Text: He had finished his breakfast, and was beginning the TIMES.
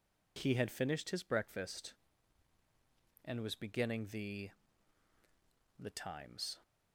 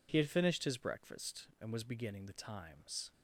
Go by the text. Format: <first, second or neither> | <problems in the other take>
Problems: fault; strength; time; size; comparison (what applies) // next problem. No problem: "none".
second | says "the" twice; at 5.7 s